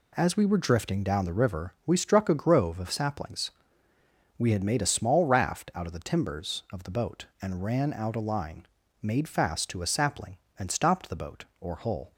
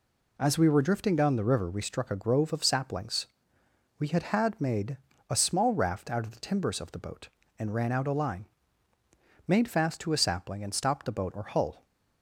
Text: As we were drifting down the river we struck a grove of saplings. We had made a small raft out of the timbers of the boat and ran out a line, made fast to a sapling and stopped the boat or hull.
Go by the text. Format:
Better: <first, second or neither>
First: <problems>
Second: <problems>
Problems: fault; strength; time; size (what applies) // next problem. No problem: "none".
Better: first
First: none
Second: says "had" twice; at 4.2 s // pauses between "made" and "a"; slight; at 4.9 s; 0.32 s long